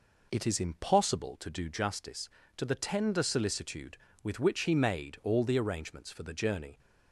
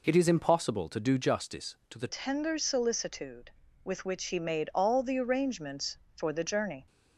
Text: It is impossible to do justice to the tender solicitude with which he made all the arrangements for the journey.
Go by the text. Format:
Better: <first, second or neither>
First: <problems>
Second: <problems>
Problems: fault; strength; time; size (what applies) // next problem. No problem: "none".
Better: first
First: none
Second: changes voice at "tender"; from 2.0 s on; 4.8 s long